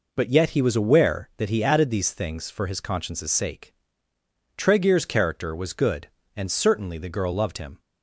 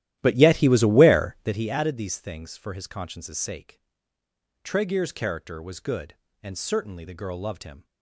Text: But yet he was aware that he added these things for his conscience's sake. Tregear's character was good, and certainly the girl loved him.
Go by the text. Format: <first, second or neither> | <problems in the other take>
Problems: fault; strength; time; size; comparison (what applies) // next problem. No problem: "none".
first | starts louder than the rest; strong; until 1.7 s; 13.5 dB